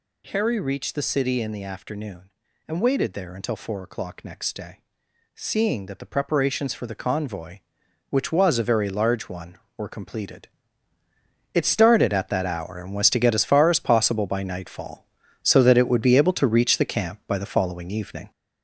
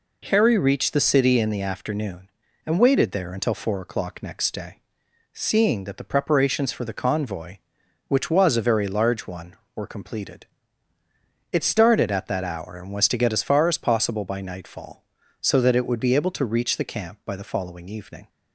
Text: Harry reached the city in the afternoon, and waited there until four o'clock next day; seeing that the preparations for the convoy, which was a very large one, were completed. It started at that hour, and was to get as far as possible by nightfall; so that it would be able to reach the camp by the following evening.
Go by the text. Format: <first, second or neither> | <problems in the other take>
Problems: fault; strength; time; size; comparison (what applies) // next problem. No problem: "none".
second | gets louder; throughout; 6.5 dB